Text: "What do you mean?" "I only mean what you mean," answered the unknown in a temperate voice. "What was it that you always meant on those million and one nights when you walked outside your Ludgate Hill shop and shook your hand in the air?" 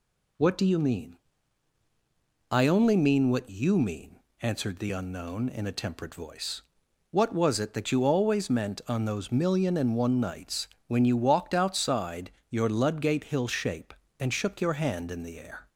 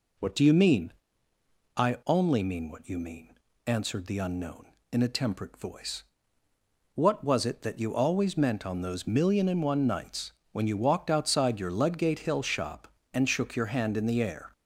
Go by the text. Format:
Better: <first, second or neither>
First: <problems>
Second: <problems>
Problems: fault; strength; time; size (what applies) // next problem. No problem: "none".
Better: second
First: pauses between "nights" and "when"; slight; at 10.6 s; 0.22 s long // pauses between "outside" and "your"; slight; at 12.3 s; 0.18 s long // says "shape" for "shop"; at 13.4 s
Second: pauses between "nights" and "when"; slight; at 10.3 s; 0.20 s long